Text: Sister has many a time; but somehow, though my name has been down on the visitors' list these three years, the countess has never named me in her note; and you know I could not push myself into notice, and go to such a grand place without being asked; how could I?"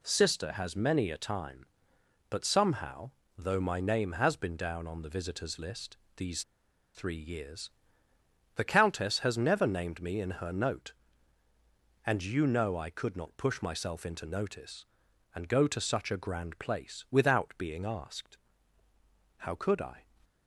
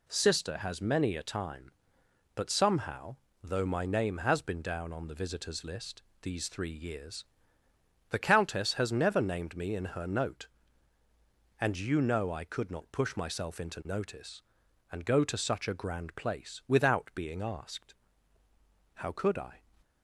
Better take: second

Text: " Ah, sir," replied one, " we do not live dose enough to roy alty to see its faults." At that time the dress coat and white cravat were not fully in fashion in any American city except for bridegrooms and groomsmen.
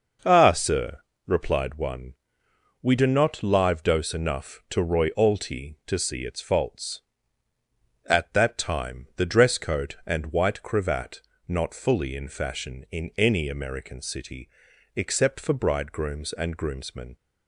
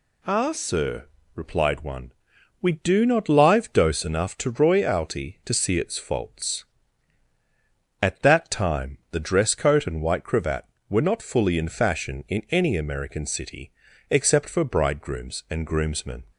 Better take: second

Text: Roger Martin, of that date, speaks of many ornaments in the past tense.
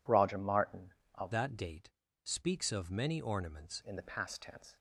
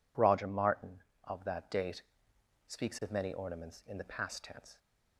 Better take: second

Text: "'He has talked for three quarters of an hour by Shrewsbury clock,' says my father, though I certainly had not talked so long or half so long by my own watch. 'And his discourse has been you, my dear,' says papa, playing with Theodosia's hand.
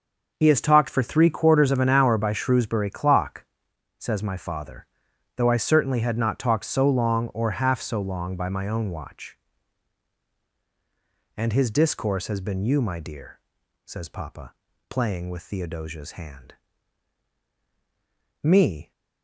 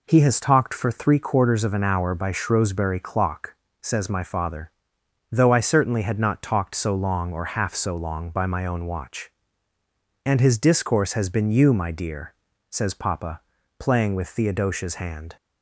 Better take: second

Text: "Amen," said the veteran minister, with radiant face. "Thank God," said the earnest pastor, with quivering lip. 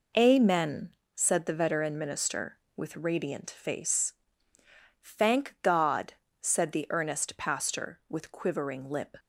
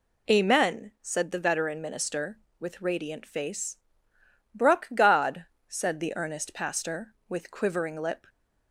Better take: first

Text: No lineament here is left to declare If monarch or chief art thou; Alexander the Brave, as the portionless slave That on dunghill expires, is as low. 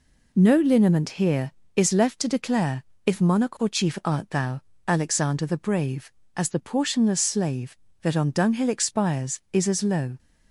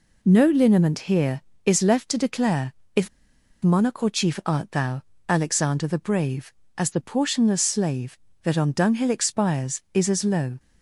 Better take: first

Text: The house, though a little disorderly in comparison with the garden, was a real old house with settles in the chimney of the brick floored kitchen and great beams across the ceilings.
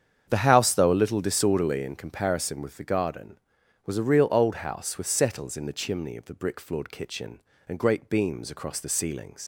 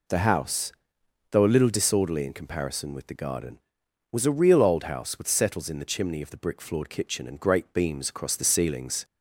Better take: second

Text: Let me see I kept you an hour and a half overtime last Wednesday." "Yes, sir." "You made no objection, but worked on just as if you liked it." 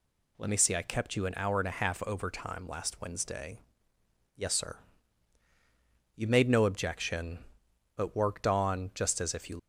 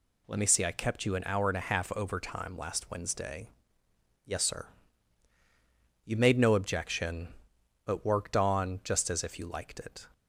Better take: second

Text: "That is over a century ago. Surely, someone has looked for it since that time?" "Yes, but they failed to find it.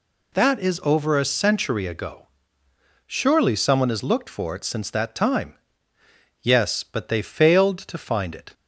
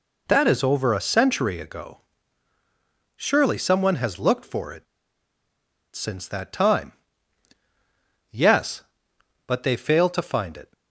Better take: first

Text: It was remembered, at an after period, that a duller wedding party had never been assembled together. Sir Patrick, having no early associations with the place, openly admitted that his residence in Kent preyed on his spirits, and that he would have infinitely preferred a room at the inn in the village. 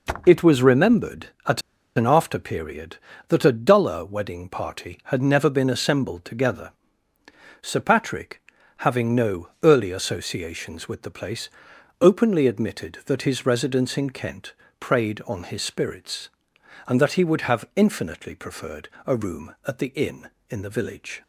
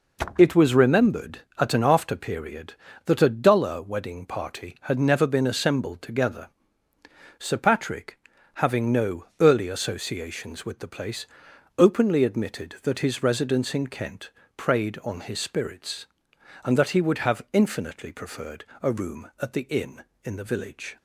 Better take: second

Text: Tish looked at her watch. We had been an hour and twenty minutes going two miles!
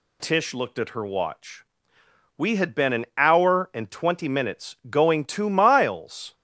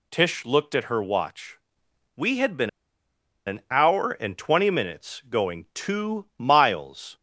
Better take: first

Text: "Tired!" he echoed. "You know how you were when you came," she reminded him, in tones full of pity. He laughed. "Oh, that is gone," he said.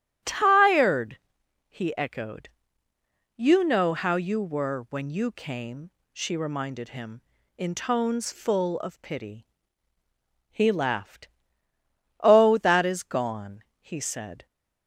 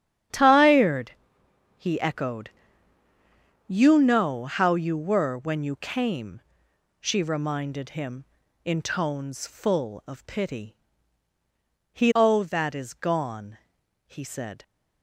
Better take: first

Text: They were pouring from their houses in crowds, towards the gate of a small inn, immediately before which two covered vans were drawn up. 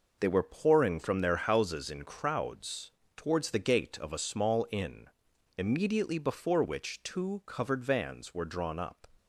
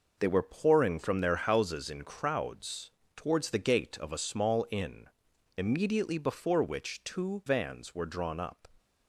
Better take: first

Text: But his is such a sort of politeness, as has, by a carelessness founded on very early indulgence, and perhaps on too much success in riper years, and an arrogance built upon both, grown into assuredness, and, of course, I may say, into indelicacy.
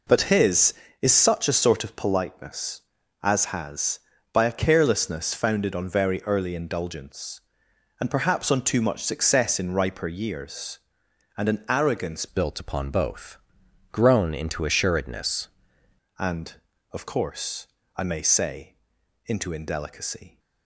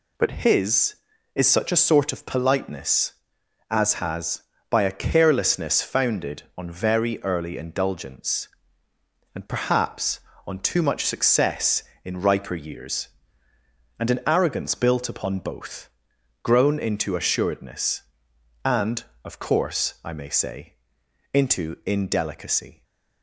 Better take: second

